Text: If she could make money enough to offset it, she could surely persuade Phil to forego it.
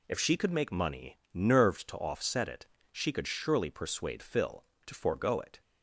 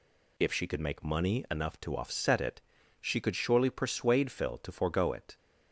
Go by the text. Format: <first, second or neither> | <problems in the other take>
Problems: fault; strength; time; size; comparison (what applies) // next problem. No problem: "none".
second | says "nerved" for "enough"; at 1.3 s